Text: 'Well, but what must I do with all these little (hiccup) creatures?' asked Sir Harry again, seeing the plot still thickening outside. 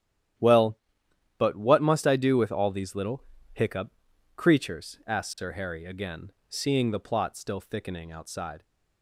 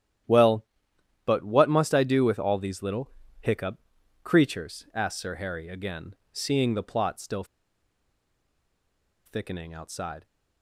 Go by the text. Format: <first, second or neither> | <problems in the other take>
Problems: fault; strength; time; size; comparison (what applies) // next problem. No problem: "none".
first | starts louder than the rest; strong; until 1.8 s; 11 dB; strong in the first // pauses between "still" and "thickening"; strong; at 7.4 s; 1.8 s long